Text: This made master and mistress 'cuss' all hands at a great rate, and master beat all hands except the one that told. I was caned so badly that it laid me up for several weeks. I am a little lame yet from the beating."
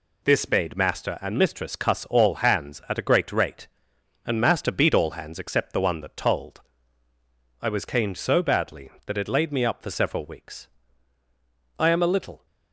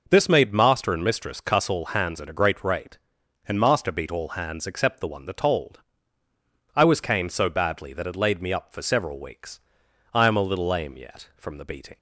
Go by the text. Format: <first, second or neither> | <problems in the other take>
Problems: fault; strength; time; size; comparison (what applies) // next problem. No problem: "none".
second | stops before "lame yet from the beating"; at 12.4 s